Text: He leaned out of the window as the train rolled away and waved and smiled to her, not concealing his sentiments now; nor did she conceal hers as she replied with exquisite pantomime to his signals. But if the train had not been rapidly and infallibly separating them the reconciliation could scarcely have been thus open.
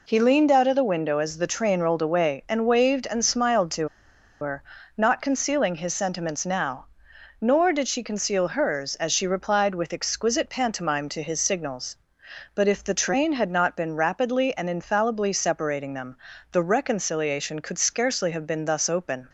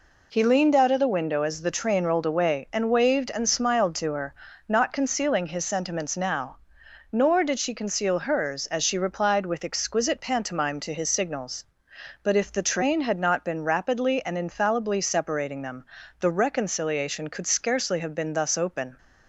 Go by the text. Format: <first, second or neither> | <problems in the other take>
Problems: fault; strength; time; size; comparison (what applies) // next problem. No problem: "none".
second | pauses between "to" and "her"; noticeable; at 3.8 s; 0.53 s long // pauses between "them" and "the"; slight; at 16.1 s; 0.34 s long; slight in the second